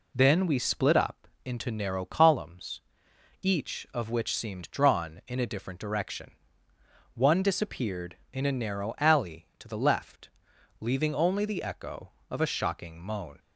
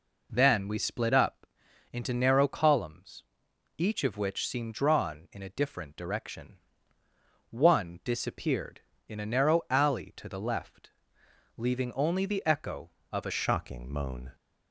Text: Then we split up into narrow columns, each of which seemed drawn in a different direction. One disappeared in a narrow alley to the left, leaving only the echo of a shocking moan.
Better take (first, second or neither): first